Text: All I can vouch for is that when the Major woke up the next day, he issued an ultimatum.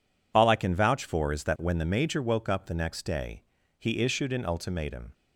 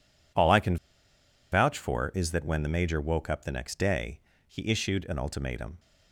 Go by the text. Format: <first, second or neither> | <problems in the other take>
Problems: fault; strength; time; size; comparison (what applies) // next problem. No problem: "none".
first | pauses between "can" and "vouch"; noticeable; at 0.7 s; 0.75 s long